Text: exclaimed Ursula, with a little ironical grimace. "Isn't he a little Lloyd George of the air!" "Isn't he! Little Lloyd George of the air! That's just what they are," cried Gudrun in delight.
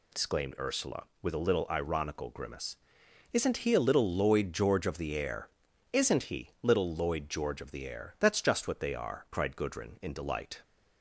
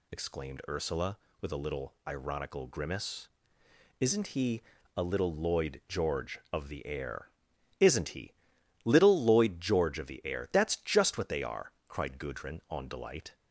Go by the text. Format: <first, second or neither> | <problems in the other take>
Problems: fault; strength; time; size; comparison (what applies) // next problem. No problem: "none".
first | pauses between "he" and "a"; slight; at 4.6 s; 0.34 s long // says "on" for "in"; at 12.7 s